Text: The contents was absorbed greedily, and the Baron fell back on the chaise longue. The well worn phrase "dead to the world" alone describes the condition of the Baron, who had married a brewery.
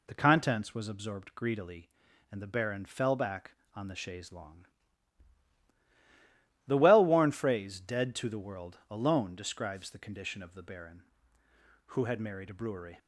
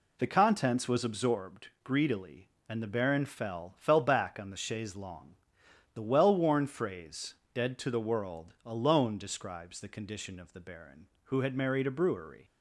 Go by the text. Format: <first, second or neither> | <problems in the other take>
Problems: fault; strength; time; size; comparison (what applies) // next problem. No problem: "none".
first | says "fell" twice; at 3.7 s // pauses between "phrase" and "dead"; slight; at 7.3 s; 0.18 s long